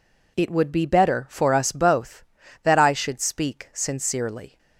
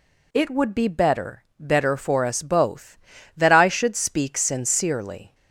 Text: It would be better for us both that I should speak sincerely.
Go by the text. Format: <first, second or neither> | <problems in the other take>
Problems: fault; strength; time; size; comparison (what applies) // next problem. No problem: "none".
first | says "better" twice; at 1.5 s